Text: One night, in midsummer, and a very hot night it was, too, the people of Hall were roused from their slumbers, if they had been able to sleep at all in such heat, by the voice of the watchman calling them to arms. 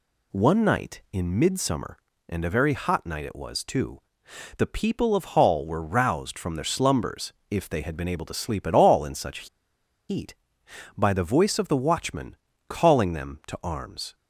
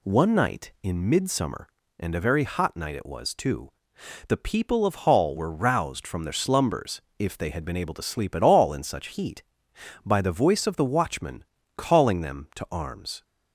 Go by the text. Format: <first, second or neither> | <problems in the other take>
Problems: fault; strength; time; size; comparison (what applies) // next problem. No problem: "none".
second | pauses between "such" and "heat"; noticeable; at 9.4 s; 0.61 s long // pauses between "watchman" and "calling"; slight; at 12.3 s; 0.32 s long; slight in the second